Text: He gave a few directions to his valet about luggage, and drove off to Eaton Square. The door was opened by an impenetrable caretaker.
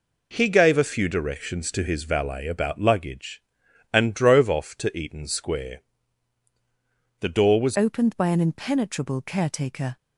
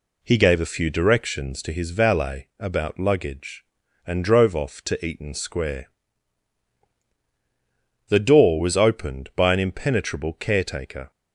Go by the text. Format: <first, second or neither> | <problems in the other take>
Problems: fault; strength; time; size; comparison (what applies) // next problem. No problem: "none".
second | changes voice at "opened"; from 7.7 s on; 2.2 s long